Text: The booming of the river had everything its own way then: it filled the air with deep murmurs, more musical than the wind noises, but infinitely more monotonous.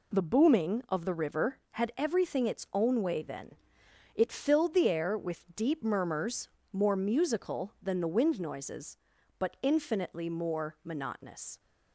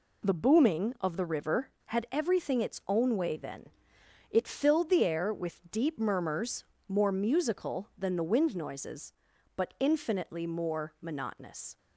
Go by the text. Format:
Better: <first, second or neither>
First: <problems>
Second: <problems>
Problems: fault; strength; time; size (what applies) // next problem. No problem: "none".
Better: neither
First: none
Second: none